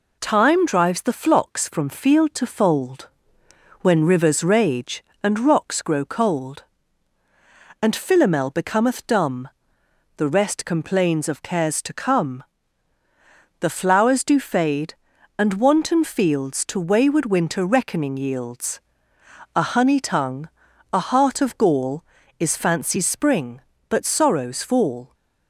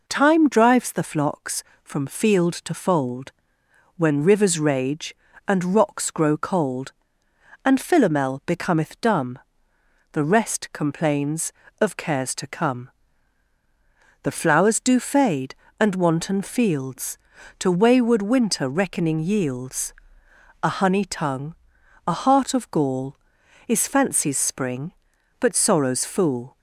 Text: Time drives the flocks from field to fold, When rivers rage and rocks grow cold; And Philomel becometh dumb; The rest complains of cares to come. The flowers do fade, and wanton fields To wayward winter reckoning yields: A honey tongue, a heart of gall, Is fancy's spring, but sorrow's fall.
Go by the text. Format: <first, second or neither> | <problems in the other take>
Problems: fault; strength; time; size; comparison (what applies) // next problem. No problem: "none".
first | says "fool" for "fall"; at 26.0 s